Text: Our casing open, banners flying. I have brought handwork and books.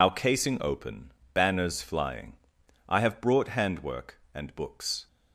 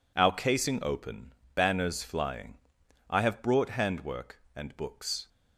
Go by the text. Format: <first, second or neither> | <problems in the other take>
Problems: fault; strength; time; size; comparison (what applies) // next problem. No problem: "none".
second | loses the start of "Our"; at 0.0 s; 65 ms